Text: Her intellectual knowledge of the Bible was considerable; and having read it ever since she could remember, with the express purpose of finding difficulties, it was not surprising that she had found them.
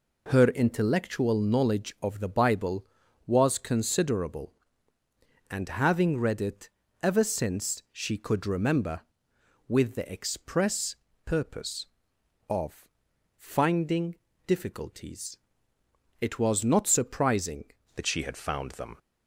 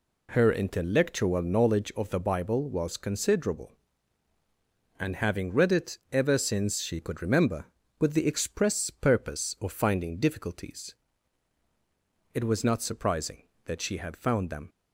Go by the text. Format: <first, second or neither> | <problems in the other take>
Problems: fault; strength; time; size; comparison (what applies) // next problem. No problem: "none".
second | pauses between "it" and "ever"; slight; at 6.6 s; 0.32 s long // pauses between "express" and "purpose"; slight; at 10.9 s; 0.28 s long // pauses between "of" and "finding"; noticeable; at 12.8 s; 0.48 s long // pauses between "finding" and "difficulties"; slight; at 14.1 s; 0.30 s long // changes voice at "that"; from 17.9 s on; 1.0 s long